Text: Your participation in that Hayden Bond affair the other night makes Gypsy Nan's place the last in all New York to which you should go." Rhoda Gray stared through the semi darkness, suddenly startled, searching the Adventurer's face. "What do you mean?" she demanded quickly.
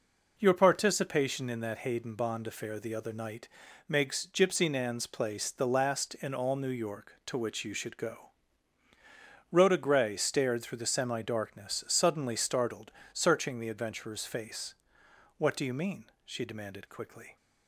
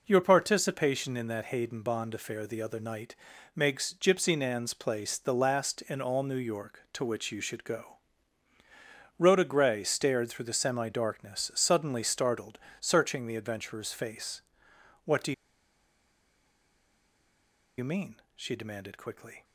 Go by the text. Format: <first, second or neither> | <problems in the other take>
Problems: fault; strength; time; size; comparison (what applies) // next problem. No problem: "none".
first | pauses between "night" and "makes"; at 3.1 s; 0.40 s long; also in the first // pauses between "do" and "you"; strong; at 15.3 s; 2.4 s long